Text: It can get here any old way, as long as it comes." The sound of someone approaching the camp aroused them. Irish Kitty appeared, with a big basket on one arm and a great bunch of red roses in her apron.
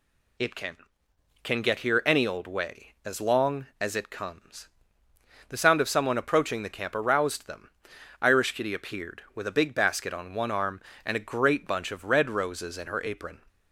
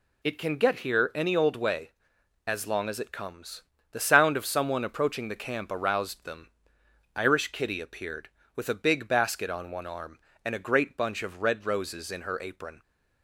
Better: second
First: says "can" twice; at 1.4 s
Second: none

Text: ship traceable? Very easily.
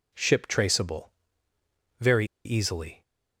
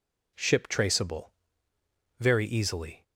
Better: second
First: pauses between "Very" and "easily"; slight; at 2.2 s; 0.19 s long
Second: none

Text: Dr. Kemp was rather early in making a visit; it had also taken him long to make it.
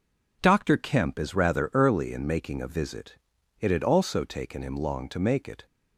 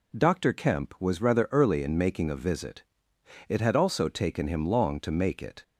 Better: second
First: says "is" for "was"; at 1.1 s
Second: none

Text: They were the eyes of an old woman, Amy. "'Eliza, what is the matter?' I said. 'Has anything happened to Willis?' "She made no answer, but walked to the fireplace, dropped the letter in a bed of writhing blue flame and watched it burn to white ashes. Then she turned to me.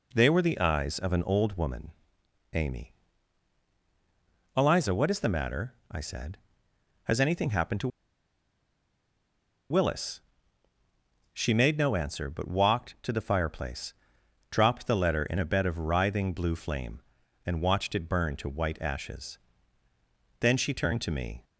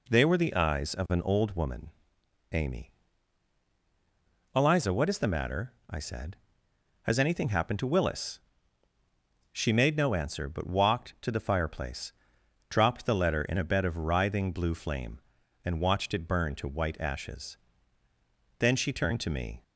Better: second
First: pauses between "to" and "Willis"; strong; at 7.8 s; 1.8 s long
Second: none

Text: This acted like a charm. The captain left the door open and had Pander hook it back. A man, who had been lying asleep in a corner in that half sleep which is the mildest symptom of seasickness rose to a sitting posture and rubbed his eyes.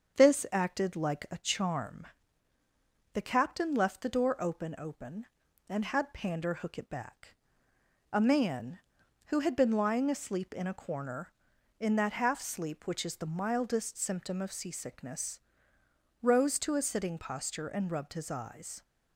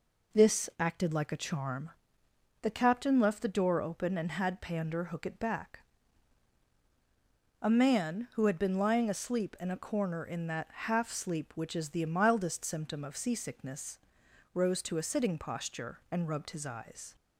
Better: second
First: starts louder than the rest; until 1.2 s; 7 dB // says "open" twice; at 4.7 s // pauses between "seasickness" and "rose"; noticeable; at 15.3 s; 0.82 s long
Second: pauses between "seasickness" and "rose"; noticeable; at 13.9 s; 0.54 s long

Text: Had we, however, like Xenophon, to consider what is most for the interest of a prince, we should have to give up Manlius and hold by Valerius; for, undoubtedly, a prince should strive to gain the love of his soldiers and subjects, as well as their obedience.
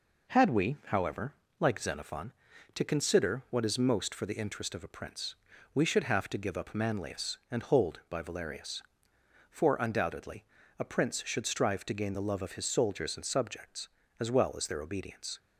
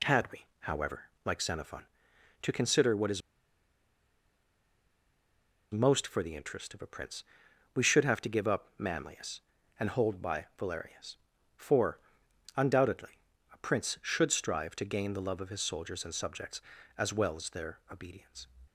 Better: first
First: none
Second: pauses between "is" and "most"; strong; at 3.2 s; 2.5 s long

